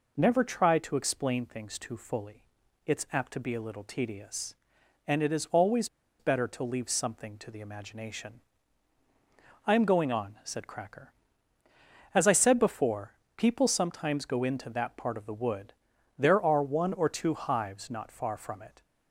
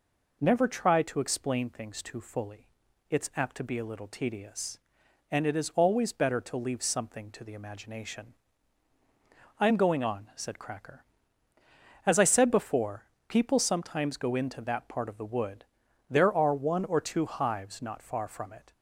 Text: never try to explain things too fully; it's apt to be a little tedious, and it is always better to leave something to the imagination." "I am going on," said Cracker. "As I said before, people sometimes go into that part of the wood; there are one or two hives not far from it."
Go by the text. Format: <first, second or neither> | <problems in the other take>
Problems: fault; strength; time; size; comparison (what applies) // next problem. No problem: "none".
second | pauses between "always" and "better"; slight; at 5.8 s; 0.32 s long